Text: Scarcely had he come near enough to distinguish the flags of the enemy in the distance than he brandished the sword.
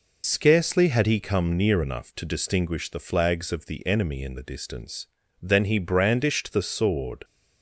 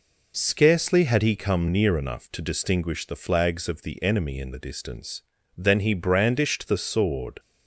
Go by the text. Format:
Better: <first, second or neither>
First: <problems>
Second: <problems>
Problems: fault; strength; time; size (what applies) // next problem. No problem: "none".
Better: second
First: loses the start of "Scarcely"; at 0.2 s; 55 ms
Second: none